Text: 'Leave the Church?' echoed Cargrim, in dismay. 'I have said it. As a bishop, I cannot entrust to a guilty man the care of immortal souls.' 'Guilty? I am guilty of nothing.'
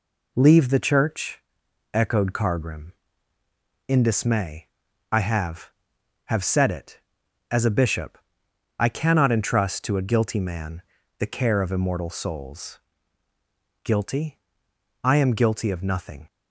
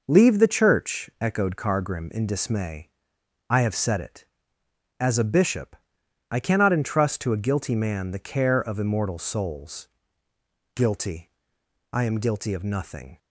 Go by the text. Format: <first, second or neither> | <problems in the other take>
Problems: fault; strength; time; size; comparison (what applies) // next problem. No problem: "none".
second | says "have" twice; at 6.2 s // pauses between "man" and "the"; slight; at 10.8 s; 0.34 s long